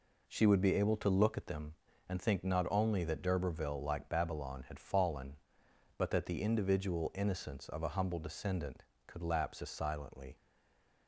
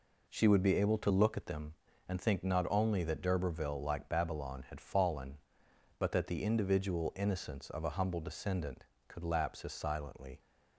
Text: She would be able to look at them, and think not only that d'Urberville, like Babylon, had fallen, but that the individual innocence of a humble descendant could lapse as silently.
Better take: second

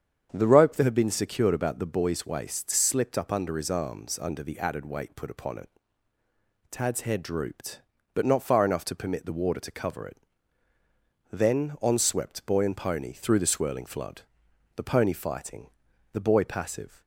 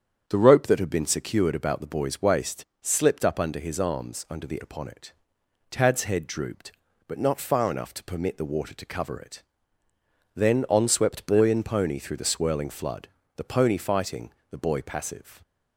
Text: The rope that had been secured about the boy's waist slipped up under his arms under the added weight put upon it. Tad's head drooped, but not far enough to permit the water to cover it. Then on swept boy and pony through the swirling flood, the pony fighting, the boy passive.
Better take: first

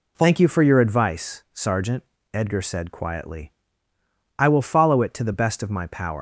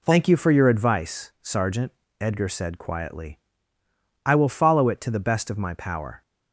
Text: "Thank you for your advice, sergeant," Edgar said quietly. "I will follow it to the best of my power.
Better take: second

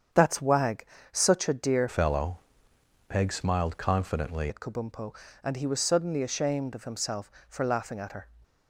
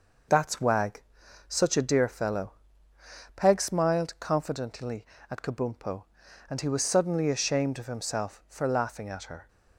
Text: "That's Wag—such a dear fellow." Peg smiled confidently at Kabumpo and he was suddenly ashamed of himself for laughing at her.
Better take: second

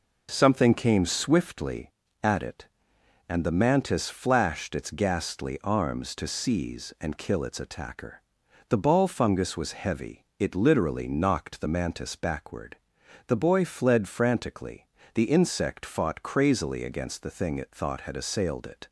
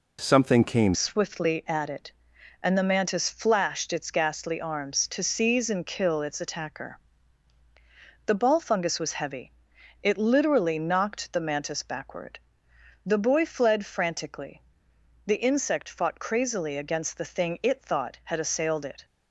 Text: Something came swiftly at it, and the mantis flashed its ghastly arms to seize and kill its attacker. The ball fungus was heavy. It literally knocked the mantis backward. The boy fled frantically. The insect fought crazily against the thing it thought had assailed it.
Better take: first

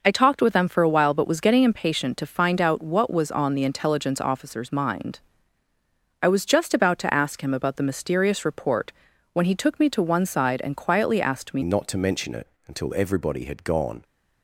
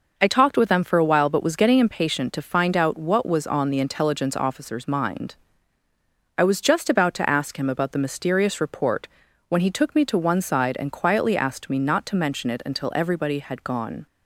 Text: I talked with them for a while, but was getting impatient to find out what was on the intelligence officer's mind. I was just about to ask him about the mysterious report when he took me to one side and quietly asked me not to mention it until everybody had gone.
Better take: second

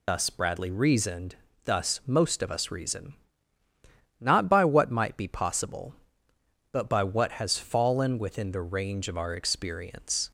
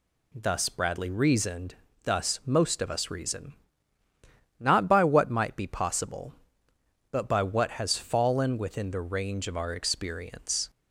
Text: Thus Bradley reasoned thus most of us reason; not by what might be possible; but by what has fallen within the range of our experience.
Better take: second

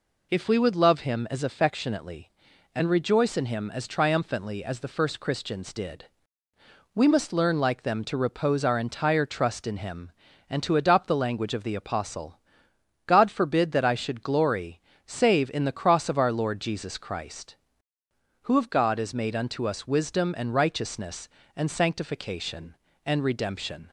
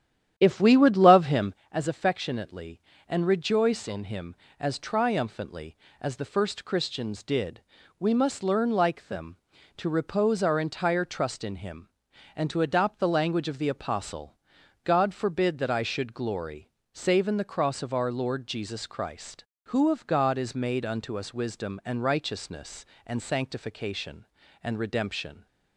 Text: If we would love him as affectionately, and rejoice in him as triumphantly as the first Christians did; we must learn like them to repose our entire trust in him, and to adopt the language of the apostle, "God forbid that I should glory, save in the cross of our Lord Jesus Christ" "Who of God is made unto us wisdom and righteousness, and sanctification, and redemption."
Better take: first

